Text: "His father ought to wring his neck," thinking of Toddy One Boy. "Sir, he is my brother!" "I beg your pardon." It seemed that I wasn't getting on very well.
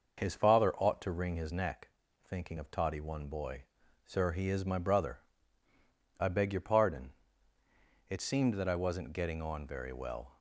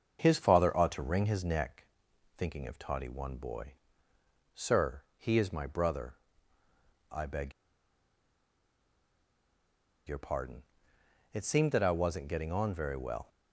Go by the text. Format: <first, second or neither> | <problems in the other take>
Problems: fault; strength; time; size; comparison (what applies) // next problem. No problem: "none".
first | starts louder than the rest; until 1.2 s; 7 dB // pauses between "beg" and "your"; strong; at 7.5 s; 2.5 s long